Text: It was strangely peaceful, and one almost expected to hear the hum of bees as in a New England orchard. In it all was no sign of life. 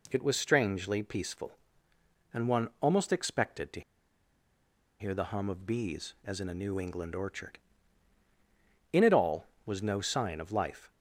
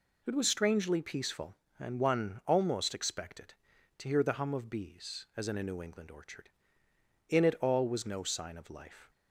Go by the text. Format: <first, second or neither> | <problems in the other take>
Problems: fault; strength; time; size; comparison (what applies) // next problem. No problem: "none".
second | pauses between "to" and "hear"; at 3.8 s; 1.1 s long